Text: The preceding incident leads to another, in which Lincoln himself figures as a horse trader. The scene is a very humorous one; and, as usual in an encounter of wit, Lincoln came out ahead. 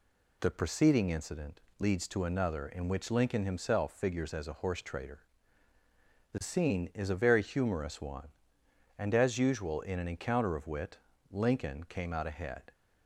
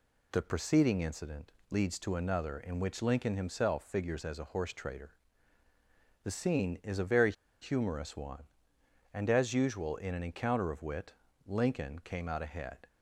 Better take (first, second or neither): first